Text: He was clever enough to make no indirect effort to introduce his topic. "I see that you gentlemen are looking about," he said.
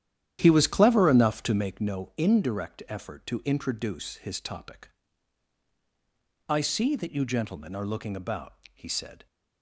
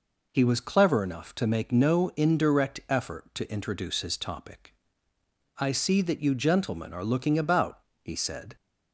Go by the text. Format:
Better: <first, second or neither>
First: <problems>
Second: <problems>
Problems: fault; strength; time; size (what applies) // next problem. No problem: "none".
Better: second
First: starts louder than the rest; strong; until 1.8 s; 11 dB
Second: none